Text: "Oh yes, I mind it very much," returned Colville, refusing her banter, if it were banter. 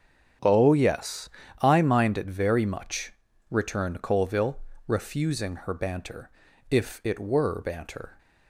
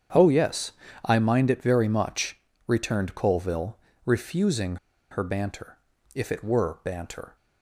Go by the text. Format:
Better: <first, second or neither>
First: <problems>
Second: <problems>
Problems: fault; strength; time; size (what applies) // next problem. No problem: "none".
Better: first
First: starts louder than the rest; strong; until 1.7 s; 8 dB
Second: starts louder than the rest; strong; until 1.4 s; 8 dB // pauses between "refusing" and "her"; slight; at 4.7 s; 0.33 s long